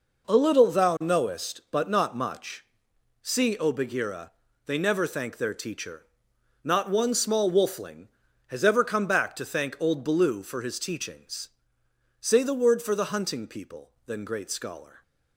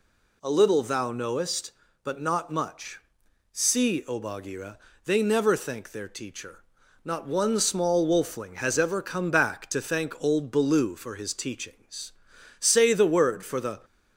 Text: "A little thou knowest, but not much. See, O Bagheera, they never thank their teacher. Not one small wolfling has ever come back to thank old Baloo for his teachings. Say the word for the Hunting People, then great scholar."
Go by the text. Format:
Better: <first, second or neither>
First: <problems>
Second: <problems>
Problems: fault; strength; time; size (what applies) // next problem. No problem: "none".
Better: first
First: none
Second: stops before "Hunting People then great scholar"; at 13.8 s